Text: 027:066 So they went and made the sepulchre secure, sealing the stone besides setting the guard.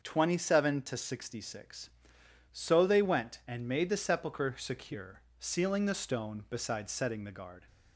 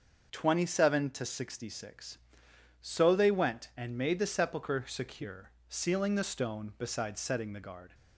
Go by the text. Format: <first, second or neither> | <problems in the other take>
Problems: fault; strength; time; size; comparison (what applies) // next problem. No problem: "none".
neither | starts louder than the rest; the same in both